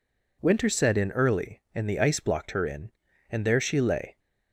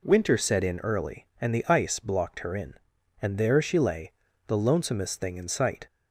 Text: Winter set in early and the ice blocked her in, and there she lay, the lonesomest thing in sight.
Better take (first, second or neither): second